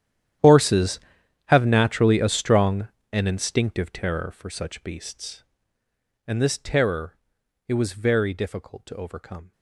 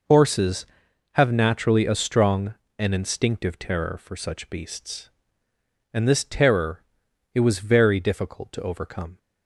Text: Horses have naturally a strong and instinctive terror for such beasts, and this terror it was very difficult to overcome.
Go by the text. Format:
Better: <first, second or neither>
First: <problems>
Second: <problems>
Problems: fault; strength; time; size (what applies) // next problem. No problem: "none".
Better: second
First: gets quieter; strong; throughout; 19.5 dB // pauses between "terror" and "it"; noticeable; at 7.1 s; 0.50 s long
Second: pauses between "terror" and "it"; noticeable; at 6.8 s; 0.50 s long